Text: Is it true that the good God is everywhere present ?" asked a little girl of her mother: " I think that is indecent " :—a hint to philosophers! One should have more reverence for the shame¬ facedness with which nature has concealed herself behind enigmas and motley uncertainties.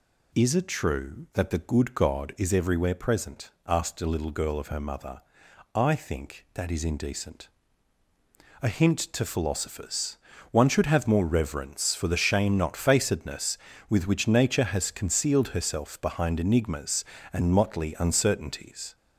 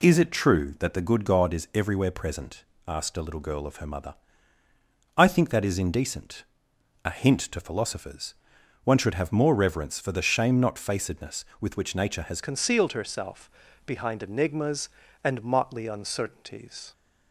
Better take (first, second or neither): first